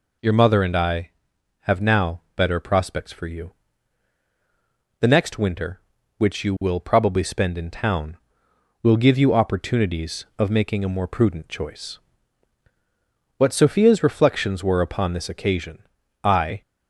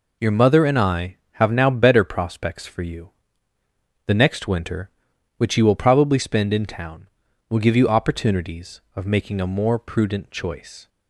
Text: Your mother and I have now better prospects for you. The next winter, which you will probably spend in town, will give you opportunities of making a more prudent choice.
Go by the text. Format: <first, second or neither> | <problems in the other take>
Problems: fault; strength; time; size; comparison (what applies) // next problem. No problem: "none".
second | goes on to say "What Sophia's reflections were upon this occasion I"; strong; from 13.3 s on; 3.2 s long